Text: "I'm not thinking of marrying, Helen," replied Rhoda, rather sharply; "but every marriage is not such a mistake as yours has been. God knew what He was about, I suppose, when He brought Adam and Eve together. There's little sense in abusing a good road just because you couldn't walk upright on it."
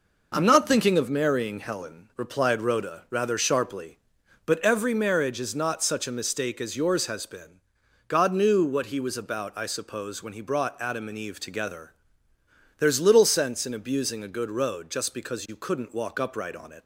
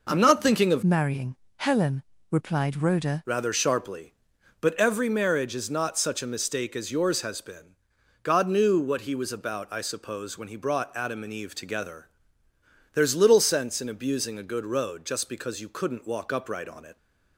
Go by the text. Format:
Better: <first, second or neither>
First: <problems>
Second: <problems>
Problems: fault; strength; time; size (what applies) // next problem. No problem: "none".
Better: first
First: none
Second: changes voice from "marrying" to "Rhoda"; from 0.8 to 3.2 s; 2.4 s long